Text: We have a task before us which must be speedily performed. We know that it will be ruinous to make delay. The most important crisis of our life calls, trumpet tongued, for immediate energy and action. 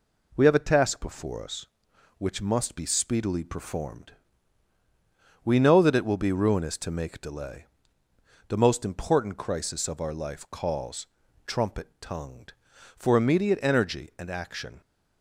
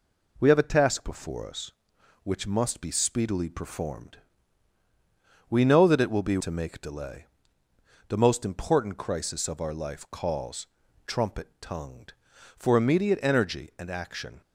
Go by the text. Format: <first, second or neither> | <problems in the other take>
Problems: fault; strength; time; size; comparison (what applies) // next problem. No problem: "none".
first | skips "ruinous"; at 6.3 s